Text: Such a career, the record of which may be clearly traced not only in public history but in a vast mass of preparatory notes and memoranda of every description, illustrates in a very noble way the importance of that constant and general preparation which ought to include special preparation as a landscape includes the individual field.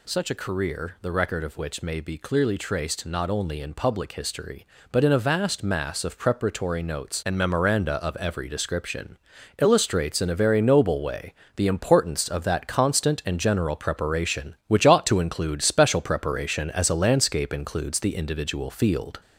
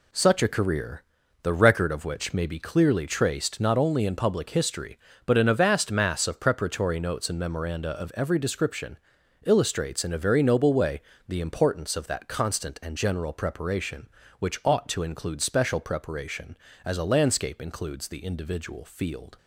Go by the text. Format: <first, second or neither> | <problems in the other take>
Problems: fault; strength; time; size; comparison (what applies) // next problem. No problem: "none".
second | gets louder; slight; throughout; 3 dB // pauses between "way" and "the"; slight; at 11.3 s; 0.24 s long; slight in the second